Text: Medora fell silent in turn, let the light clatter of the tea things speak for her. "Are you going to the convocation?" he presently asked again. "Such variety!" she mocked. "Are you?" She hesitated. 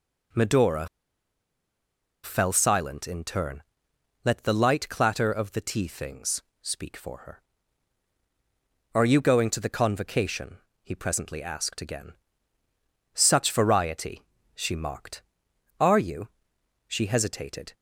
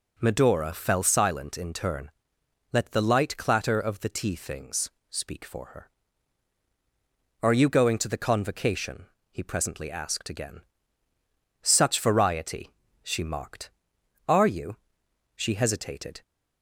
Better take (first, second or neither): second